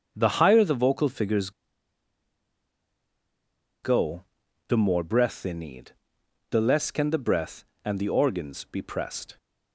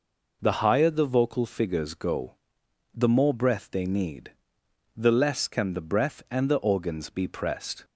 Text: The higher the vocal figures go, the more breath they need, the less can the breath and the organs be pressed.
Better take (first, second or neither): second